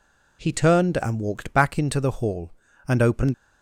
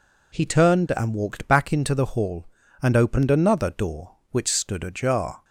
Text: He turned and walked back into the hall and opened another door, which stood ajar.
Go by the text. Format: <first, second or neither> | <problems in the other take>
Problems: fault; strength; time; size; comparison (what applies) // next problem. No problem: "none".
second | stops before "another door which stood ajar"; at 3.3 s